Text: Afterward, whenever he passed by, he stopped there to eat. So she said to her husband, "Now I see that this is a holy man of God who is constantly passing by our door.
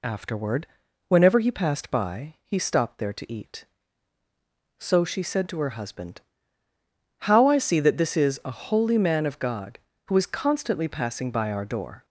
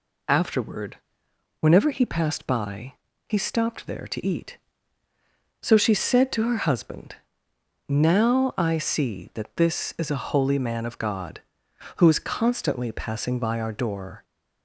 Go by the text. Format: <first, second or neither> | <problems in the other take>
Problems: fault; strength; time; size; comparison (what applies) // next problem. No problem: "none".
second | says "How" for "Now"; at 7.2 s